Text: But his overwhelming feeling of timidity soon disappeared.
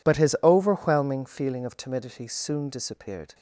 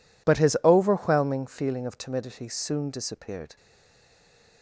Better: first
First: none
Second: stays silent after the last word; from 3.5 s on; 1.1 s long

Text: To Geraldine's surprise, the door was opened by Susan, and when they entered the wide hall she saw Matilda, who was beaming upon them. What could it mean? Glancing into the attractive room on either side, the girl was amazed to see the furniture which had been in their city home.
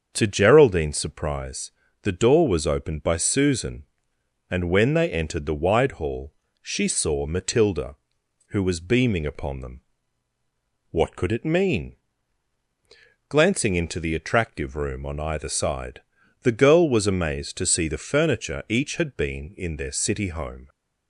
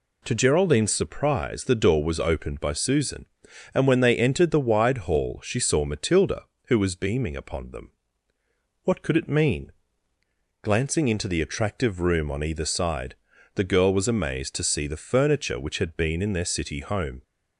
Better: second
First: starts louder than the rest; until 1.1 s; 7 dB // pauses between "hall" and "she"; slight; at 6.3 s; 0.28 s long // says "each" for "which"; at 18.6 s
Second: none

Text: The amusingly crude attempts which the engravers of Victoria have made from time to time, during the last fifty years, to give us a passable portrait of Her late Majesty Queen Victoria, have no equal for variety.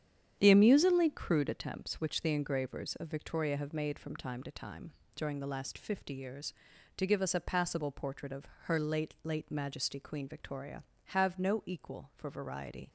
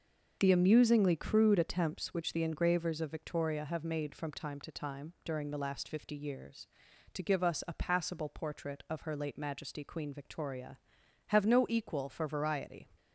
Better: second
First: starts louder than the rest; strong; until 1.3 s; 9 dB // pauses between "of" and "Her"; slight; at 8.4 s; 0.16 s long // says "late" twice; at 9.2 s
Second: starts louder than the rest; until 1.4 s; 6.5 dB

